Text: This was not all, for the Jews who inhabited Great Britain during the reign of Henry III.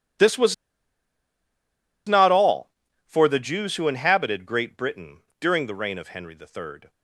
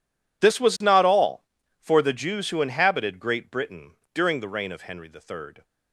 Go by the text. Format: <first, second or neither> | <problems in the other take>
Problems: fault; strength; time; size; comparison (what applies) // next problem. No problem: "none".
second | pauses between "was" and "not"; strong; at 0.5 s; 1.5 s long // pauses between "Britain" and "during"; slight; at 5.2 s; 0.18 s long; slight in the second